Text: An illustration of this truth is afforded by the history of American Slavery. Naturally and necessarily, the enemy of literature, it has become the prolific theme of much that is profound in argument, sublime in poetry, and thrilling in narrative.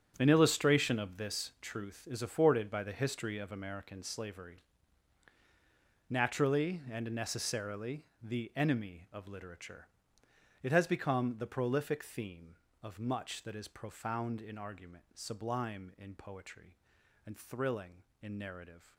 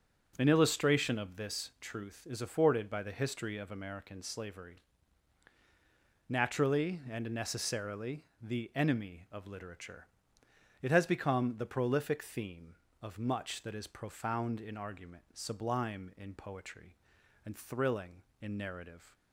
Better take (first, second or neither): second